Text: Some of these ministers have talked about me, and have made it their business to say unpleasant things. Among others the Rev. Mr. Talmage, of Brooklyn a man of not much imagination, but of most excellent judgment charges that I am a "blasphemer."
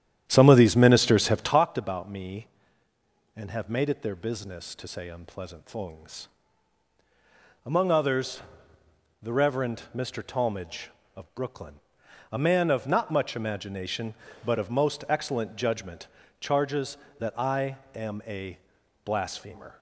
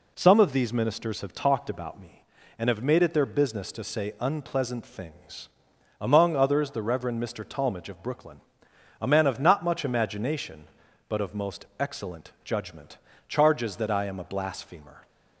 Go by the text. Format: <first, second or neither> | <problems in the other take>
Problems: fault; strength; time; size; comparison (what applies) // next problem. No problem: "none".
second | starts louder than the rest; strong; until 1.6 s; 10.5 dB // pauses between "others" and "the"; noticeable; at 8.4 s; 0.80 s long // pauses between "Brooklyn" and "a"; noticeable; at 11.7 s; 0.56 s long; noticeable in the second // pauses between "judgment" and "charges"; slight; at 16.0 s; 0.32 s long; slight in the second // pauses between "I" and "am"; slight; at 17.7 s; 0.16 s long // pauses between "a" and "blasphemer"; noticeable; at 18.5 s; 0.46 s long